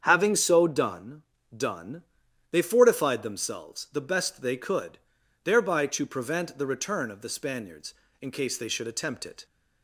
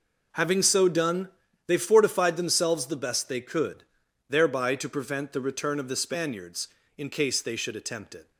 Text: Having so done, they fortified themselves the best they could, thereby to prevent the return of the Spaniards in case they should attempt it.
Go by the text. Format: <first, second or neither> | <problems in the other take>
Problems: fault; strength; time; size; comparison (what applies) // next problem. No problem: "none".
second | starts louder than the rest; strong; until 1.0 s; 7.5 dB // says "done" twice; at 1.5 s